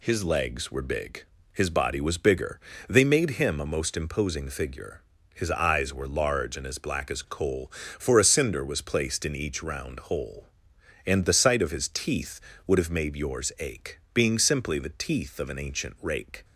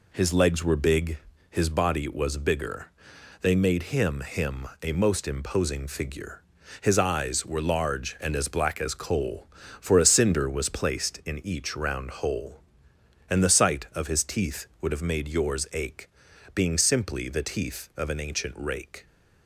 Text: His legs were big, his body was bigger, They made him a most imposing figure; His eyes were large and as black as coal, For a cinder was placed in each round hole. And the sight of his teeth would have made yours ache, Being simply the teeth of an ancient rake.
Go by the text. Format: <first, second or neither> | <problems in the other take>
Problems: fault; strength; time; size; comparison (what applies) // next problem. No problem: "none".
first | says "him" twice; at 4.2 s